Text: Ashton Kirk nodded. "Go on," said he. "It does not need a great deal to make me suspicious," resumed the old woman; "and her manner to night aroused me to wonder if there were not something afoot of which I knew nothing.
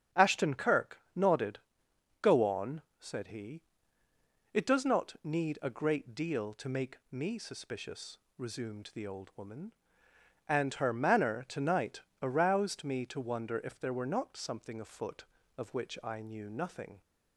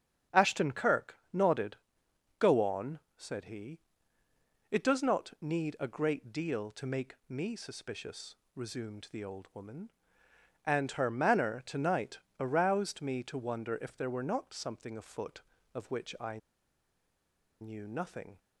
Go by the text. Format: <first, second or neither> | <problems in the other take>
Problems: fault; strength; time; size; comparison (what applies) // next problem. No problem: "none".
first | starts louder than the rest; strong; until 1.4 s; 8 dB; strong in the first // pauses between "Kirk" and "nodded"; slight; at 1.1 s; 0.16 s long; slight in the first // pauses between "night" and "aroused"; slight; at 12.1 s; 0.20 s long; slight in the first // pauses between "I" and "knew"; at 16.3 s; 1.2 s long